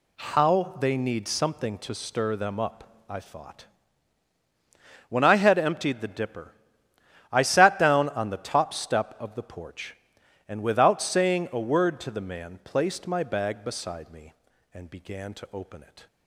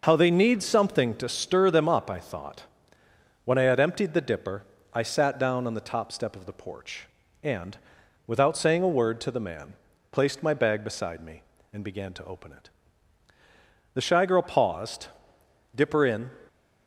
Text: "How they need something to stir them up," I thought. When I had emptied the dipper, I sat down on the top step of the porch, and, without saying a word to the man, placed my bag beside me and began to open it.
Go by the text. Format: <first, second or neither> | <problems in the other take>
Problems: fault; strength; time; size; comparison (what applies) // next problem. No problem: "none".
first | goes on to say "The shy girl paused dipper in"; strong; from 13.9 s on; 2.3 s long